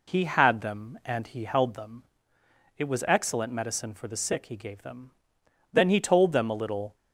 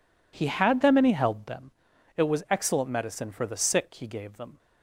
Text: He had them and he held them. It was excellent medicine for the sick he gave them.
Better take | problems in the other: second | goes on to say "Then he told them a little"; noticeable; from 5.7 s on; 1.2 s long

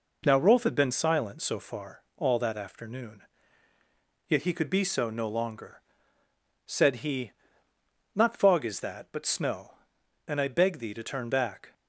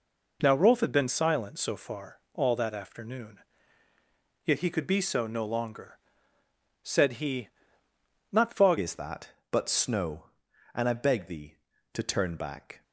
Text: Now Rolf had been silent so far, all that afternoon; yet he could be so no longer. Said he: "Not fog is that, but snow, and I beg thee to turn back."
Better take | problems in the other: first | changes voice at "is"; from 8.7 s on; 4.1 s long

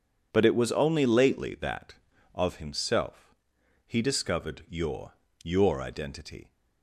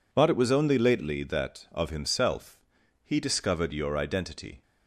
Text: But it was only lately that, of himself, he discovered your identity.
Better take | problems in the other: second | says "your" twice; at 5.4 s

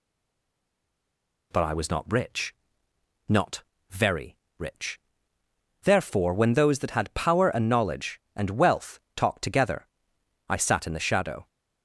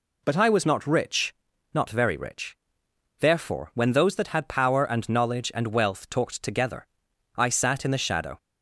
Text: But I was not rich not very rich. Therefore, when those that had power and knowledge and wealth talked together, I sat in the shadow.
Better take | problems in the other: second | stays silent before the first word; noticeable; until 1.5 s; 1.5 s long // pauses between "rich" and "not"; noticeable; at 2.5 s; 0.74 s long; also in the second // pauses between "not" and "very"; slight; at 3.6 s; 0.28 s long // pauses between "very" and "rich"; slight; at 4.3 s; 0.24 s long // pauses between "wealth" and "talked"; slight; at 8.9 s; 0.16 s long

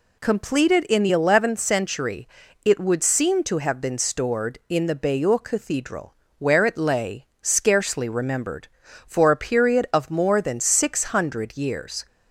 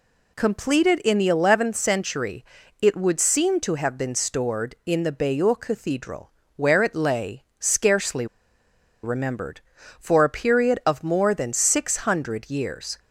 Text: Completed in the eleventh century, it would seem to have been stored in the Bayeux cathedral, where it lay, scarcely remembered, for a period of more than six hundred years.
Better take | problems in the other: first | pauses between "scarcely" and "remembered"; noticeable; at 8.2 s; 0.77 s long

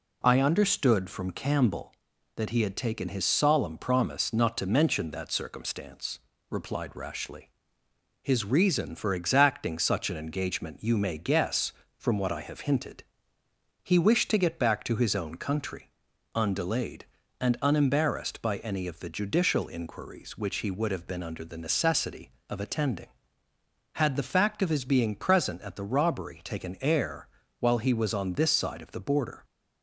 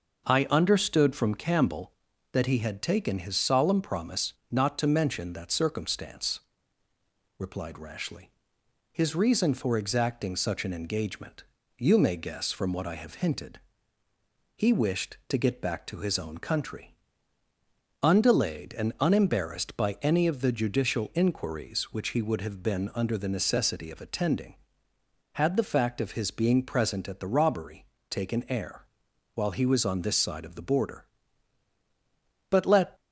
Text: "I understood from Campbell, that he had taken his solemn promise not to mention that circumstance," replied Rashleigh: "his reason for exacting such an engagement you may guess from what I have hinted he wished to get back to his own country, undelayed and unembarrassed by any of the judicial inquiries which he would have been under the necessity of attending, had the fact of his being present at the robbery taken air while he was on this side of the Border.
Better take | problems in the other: first | starts louder than the rest; noticeable; until 1.3 s; 6 dB // pauses between "promise" and "not"; slight; at 4.3 s; 0.16 s long // pauses between "engagement" and "you"; slight; at 11.4 s; 0.34 s long // pauses between "hinted" and "he"; noticeable; at 13.5 s; 0.96 s long; noticeable in the first // pauses between "robbery" and "taken"; slight; at 27.8 s; 0.26 s long // pauses between "air" and "while"; noticeable; at 28.8 s; 0.48 s long; slight in the first // goes on to say "But let"; slight; from 32.5 s on; 0.48 s long

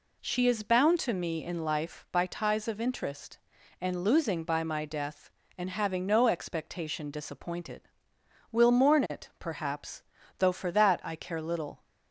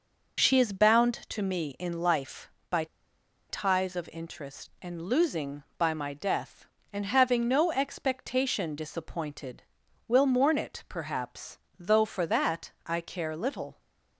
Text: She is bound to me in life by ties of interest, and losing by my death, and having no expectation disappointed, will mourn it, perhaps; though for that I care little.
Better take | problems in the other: first | pauses between "by" and "ties"; noticeable; at 2.8 s; 0.64 s long

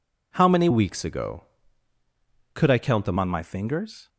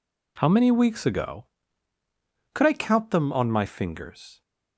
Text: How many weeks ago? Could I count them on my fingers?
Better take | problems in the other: second | changes voice from "weeks" to "them"; from 0.7 to 3.1 s; 2.4 s long

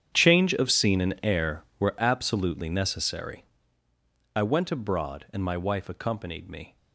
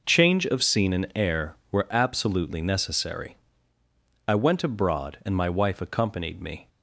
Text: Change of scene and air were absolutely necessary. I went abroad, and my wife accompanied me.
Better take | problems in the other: second | gets quieter; strong; throughout; 16.5 dB

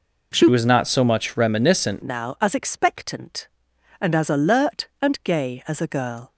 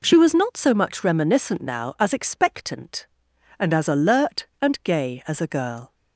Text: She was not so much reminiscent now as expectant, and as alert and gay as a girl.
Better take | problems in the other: second | changes voice from "was" to "reminiscent"; from 0.5 to 2.0 s; 1.5 s long

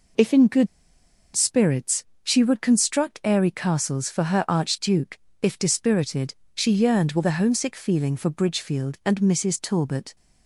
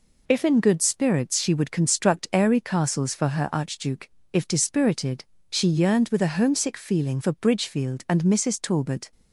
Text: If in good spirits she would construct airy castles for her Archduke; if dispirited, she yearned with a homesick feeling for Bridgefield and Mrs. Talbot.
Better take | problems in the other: second | pauses between "good" and "spirits"; noticeable; at 0.6 s; 0.68 s long // pauses between "spirits" and "she"; slight; at 2.0 s; 0.18 s long

